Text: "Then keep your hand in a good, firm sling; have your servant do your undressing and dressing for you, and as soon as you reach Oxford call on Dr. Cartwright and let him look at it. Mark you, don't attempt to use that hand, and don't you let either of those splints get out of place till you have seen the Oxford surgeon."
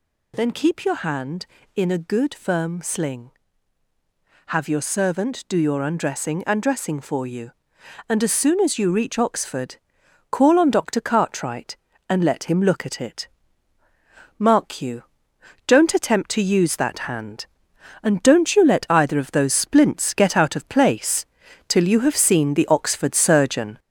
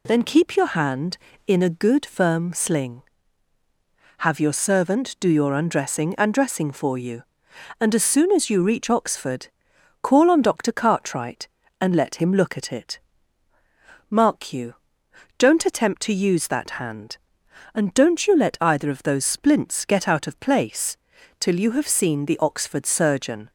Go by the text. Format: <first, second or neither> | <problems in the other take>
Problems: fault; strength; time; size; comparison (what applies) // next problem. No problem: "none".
second | gets louder; noticeable; throughout; 4.5 dB // pauses between "Oxford" and "call"; noticeable; at 9.7 s; 0.54 s long; noticeable in the second // pauses between "place" and "till"; at 21.2 s; 0.44 s long; also in the second